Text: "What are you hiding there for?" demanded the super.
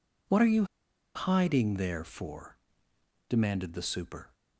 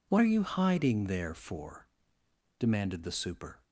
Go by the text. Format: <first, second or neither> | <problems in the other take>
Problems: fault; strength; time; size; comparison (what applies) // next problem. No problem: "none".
second | pauses between "you" and "hiding"; noticeable; at 0.6 s; 0.49 s long